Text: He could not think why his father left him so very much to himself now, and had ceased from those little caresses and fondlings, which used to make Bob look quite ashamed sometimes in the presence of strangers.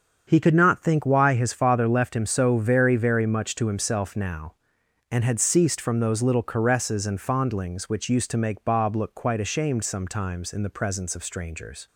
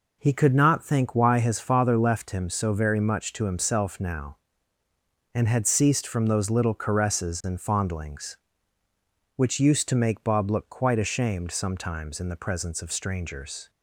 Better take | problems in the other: second | starts louder than the rest; until 1.3 s; 7 dB // says "very" twice; at 2.9 s

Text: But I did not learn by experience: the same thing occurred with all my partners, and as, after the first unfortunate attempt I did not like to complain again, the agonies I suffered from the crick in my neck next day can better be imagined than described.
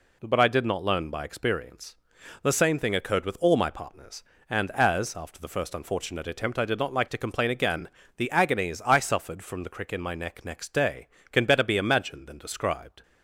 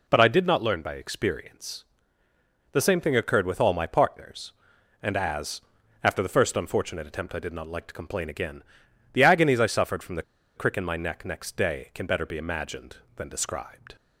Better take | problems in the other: first | pauses between "the" and "crick"; slight; at 10.2 s; 0.34 s long

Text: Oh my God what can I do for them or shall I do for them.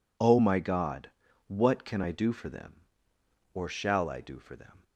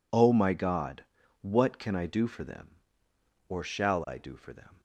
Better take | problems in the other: neither | pauses between "God" and "what"; the same in both

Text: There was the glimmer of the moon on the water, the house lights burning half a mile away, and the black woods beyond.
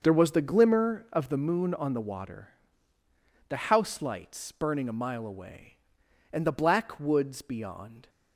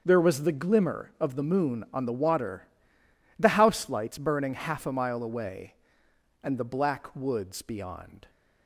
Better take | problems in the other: second | starts louder than the rest; until 1.0 s; 6.5 dB; also in the second // skips "half"; at 4.8 s

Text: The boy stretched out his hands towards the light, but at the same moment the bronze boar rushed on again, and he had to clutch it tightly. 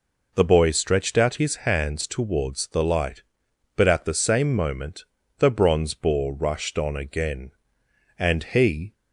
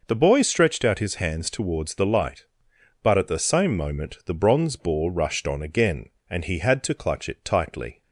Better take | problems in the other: second | pauses between "moment" and "the"; slight; at 5.0 s; 0.36 s long // stops before "had to clutch it tightly"; at 8.9 s

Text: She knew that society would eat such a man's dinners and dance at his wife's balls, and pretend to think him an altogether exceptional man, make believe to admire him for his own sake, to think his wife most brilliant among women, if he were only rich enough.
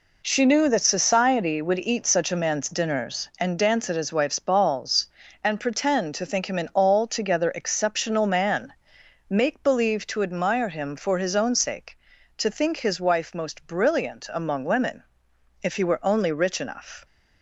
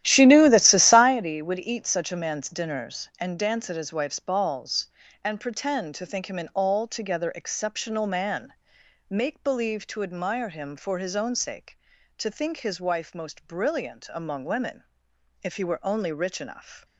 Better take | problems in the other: first | starts louder than the rest; strong; until 1.1 s; 13 dB

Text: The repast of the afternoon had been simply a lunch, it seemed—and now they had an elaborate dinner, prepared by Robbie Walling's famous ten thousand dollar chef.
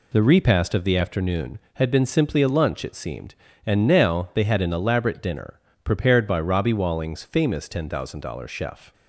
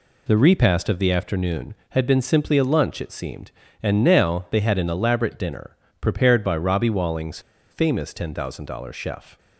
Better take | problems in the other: first | pauses between "Walling's" and "famous"; slight; at 7.3 s; 0.31 s long

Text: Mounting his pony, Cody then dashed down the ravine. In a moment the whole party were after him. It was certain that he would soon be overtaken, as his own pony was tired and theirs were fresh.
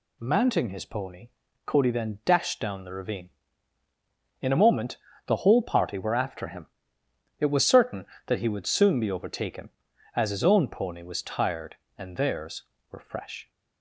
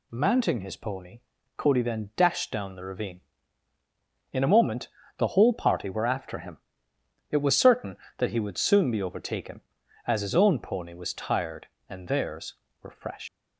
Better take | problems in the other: first | pauses between "moment" and "the"; slight; at 4.8 s; 0.30 s long; slight in the first // leaves "fresh" unfinished; at 13.2 s; 135 ms

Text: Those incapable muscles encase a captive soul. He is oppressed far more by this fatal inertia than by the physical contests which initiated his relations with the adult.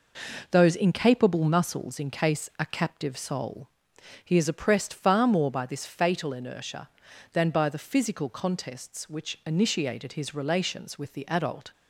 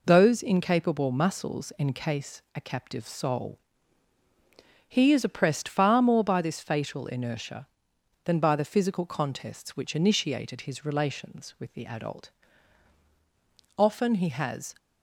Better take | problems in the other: first | goes on to say "Often he has"; noticeable; from 13.7 s on; 0.98 s long

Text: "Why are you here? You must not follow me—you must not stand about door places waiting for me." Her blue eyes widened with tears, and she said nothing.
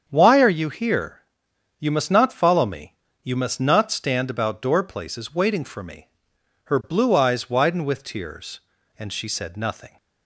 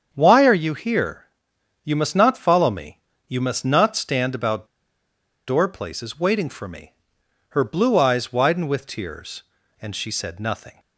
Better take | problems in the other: first | starts louder than the rest; strong; until 1.1 s; 7.5 dB; strong in the first // pauses between "about" and "door"; noticeable; at 4.6 s; 0.81 s long

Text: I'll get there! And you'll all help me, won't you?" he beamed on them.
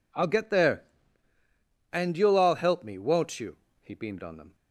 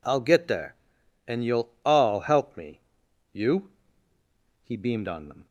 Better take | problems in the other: first | skips "won't"; at 3.0 s

